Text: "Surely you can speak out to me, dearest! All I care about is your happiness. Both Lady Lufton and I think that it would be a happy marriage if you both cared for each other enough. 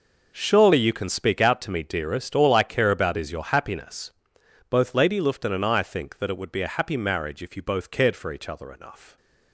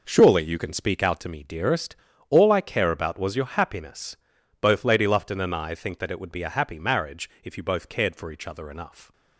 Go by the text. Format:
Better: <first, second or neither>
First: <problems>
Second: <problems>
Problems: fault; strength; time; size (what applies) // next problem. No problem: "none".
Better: first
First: none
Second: says "was" for "is"; at 3.1 s